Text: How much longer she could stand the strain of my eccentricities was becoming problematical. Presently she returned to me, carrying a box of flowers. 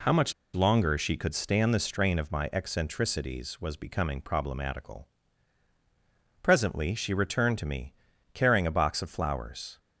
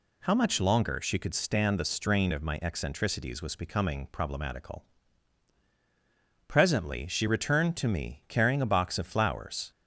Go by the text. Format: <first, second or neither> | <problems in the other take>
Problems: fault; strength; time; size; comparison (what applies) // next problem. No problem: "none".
second | pauses between "much" and "longer"; slight; at 0.3 s; 0.20 s long